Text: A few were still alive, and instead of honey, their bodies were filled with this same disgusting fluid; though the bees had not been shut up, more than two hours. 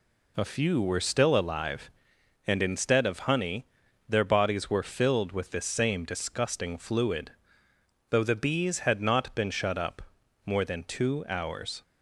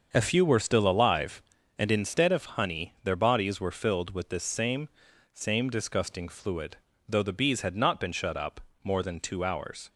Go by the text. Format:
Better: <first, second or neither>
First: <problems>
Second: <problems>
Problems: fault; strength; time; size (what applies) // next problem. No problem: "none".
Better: first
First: none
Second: starts louder than the rest; until 1.1 s; 6.5 dB // says "same" twice; at 5.3 s